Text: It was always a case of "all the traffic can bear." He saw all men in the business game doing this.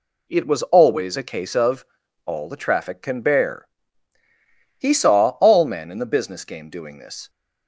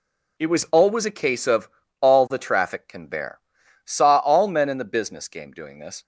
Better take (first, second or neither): first